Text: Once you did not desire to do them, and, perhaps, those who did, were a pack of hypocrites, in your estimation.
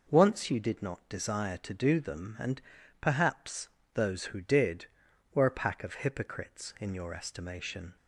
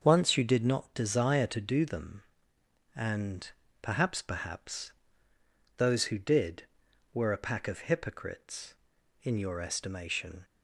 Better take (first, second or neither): first